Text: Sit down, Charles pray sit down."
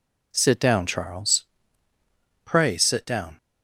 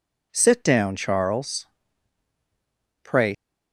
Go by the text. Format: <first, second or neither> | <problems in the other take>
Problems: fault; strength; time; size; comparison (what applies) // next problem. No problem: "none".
first | pauses between "Charles" and "pray"; strong; at 1.6 s; 1.3 s long; also in the first // stops before "sit down"; at 3.3 s